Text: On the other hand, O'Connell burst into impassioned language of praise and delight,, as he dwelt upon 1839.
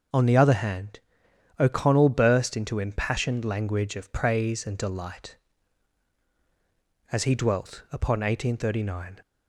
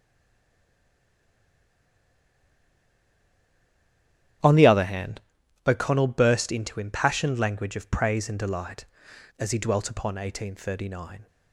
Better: first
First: none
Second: stays silent before the first word; strong; until 4.4 s; 4.4 s long // starts louder than the rest; strong; until 5.8 s; 10.5 dB

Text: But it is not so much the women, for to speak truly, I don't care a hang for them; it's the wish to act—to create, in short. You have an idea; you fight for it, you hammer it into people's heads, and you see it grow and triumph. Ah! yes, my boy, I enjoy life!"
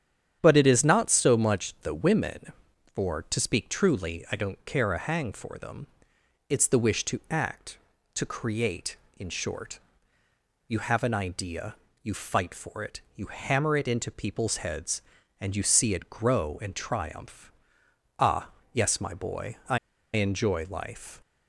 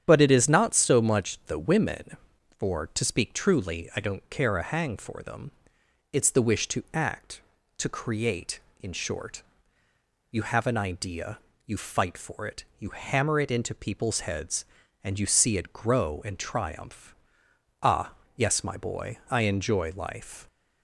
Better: second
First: starts louder than the rest; strong; until 1.4 s; 9 dB // pauses between "I" and "enjoy"; at 19.7 s; 0.36 s long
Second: starts louder than the rest; strong; until 1.0 s; 9 dB

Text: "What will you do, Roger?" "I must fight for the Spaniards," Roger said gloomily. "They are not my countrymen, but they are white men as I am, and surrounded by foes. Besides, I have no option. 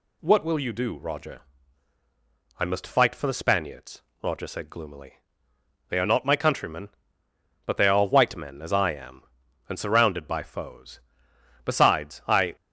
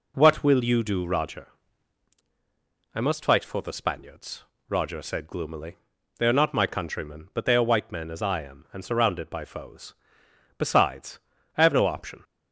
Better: second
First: stops before "have no option"; at 12.5 s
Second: none

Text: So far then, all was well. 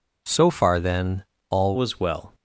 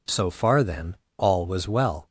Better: second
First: changes voice at "was"; from 1.7 s on; 0.6 s long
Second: none

